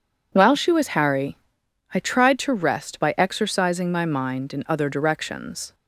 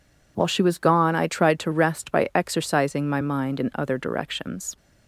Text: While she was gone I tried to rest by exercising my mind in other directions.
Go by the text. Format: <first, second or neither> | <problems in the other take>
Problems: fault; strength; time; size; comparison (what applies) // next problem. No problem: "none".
second | says "harry" for "gone"; at 0.9 s